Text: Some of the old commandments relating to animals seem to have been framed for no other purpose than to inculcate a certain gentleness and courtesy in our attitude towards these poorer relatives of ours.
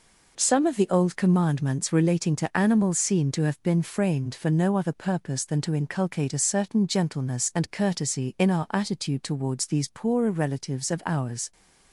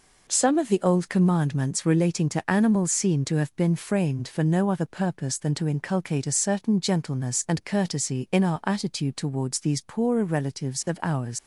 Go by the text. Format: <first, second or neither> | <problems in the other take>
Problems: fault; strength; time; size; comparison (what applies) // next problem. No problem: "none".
first | leaves "ours" unfinished; at 11.3 s; 95 ms